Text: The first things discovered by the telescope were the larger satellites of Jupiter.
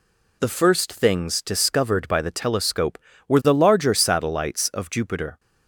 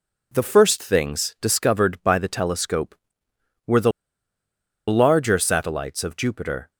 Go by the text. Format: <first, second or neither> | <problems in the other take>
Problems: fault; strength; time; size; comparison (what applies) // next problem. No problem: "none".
first | pauses between "the" and "larger"; noticeable; at 3.9 s; 0.97 s long